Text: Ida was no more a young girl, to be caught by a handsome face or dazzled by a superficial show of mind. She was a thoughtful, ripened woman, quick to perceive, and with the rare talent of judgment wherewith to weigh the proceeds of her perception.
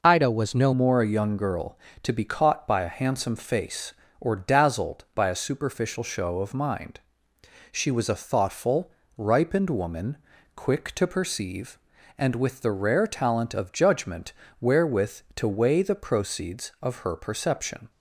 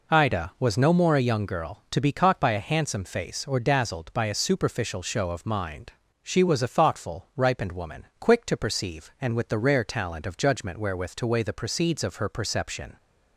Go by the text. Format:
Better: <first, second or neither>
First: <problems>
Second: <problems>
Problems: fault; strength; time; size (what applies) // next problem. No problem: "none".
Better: second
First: changes voice at "more"; from 0.7 s on; 17.2 s long // pauses between "judgment" and "wherewith"; slight; at 14.3 s; 0.28 s long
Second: none